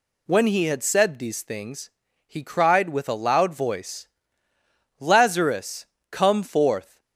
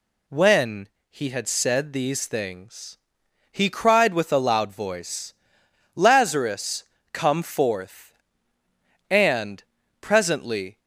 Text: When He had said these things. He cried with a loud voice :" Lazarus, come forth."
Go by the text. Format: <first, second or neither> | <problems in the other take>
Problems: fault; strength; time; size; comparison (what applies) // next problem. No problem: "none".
first | pauses between "When" and "He"; slight; at 0.8 s; 0.20 s long // goes on to say "And presently"; strong; from 9.0 s on; 1.7 s long